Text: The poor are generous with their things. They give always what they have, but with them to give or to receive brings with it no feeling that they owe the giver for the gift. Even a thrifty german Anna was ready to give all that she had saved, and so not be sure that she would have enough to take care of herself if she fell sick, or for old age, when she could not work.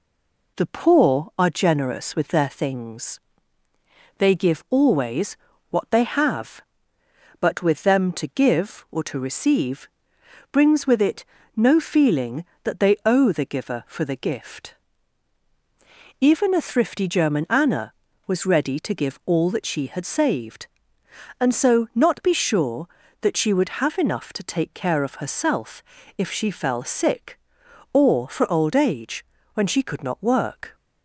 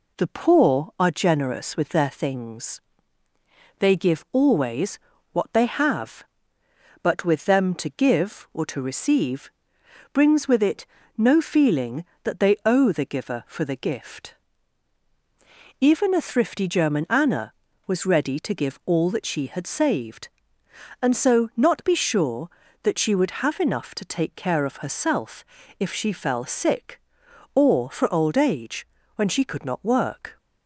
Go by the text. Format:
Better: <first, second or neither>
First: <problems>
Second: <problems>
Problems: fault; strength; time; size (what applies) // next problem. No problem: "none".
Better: second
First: stays silent before the first word; slight; until 0.5 s; 0.5 s long // pauses between "always" and "what"; slight; at 5.3 s; 0.36 s long // pauses between "receive" and "brings"; noticeable; at 9.8 s; 0.64 s long // pauses between "it" and "no"; slight; at 11.2 s; 0.32 s long // pauses between "herself" and "if"; slight; at 25.8 s; 0.36 s long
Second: pauses between "always" and "what"; slight; at 4.9 s; 0.36 s long // pauses between "receive" and "brings"; noticeable; at 9.5 s; 0.63 s long // pauses between "it" and "no"; slight; at 10.8 s; 0.32 s long // pauses between "herself" and "if"; slight; at 25.4 s; 0.36 s long